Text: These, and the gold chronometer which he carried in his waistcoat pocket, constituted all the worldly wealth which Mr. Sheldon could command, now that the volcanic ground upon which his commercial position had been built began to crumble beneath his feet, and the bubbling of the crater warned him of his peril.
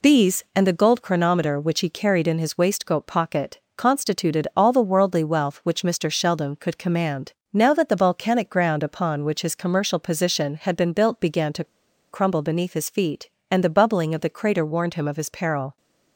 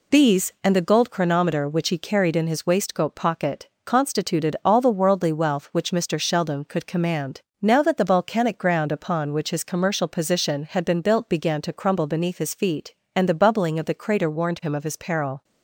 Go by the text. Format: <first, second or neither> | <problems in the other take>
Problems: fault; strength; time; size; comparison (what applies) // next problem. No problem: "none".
second | pauses between "to" and "crumble"; noticeable; at 11.6 s; 0.46 s long